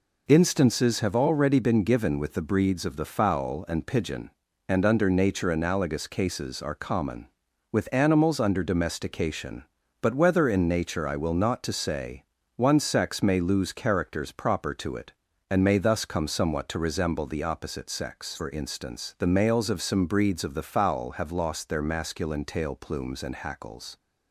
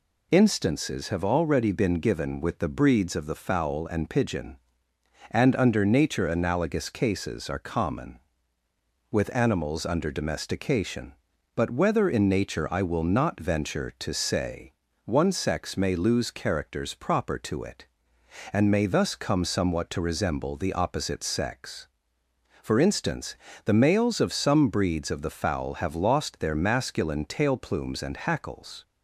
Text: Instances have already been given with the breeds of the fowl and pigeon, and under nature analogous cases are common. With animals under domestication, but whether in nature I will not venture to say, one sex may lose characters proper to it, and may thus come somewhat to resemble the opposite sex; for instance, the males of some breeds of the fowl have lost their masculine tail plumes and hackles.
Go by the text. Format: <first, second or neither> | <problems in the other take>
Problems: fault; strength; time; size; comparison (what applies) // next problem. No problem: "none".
second | skips "venture"; at 11.6 s